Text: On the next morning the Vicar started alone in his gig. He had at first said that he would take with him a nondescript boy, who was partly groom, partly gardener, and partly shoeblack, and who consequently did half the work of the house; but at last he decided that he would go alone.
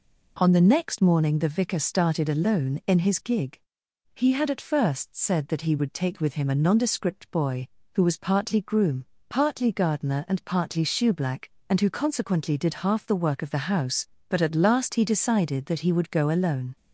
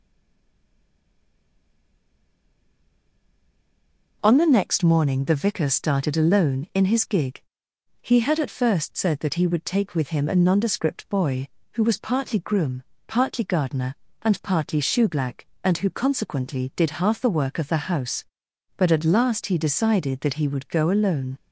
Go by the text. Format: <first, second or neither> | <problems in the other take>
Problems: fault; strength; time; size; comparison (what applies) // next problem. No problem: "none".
first | stays silent before the first word; strong; until 4.2 s; 4.2 s long